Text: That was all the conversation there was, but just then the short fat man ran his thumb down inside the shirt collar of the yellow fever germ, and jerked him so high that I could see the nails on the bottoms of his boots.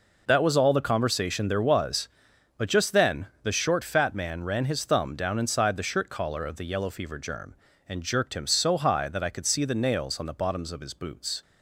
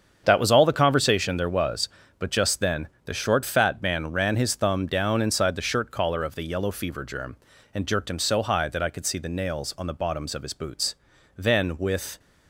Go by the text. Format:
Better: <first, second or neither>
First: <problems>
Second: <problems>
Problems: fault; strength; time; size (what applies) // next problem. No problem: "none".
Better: first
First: pauses between "then" and "the"; slight; at 3.2 s; 0.16 s long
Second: starts louder than the rest; strong; until 1.2 s; 7.5 dB // pauses between "then" and "the"; slight; at 2.8 s; 0.16 s long // goes on to say "Then with"; noticeable; from 11.3 s on; 0.82 s long